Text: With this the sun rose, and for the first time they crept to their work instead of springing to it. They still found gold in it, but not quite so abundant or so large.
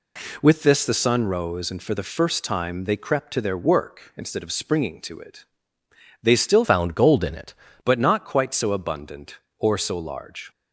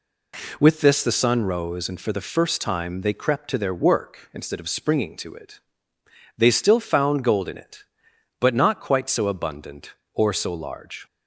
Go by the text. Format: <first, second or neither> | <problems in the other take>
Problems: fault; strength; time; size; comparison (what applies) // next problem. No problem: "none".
second | changes voice from "found" to "it"; from 6.6 to 7.5 s; 0.9 s long